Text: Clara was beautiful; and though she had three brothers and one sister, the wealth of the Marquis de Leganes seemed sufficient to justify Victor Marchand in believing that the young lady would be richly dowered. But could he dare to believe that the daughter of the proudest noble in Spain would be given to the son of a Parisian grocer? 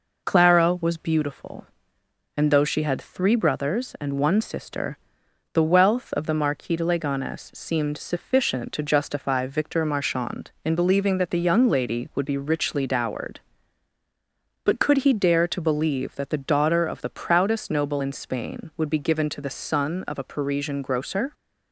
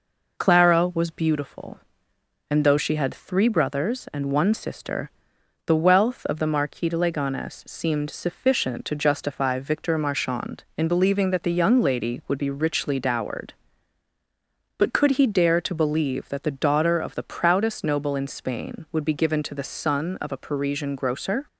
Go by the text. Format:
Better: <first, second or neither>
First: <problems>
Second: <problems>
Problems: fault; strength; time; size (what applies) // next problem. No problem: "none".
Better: neither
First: none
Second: none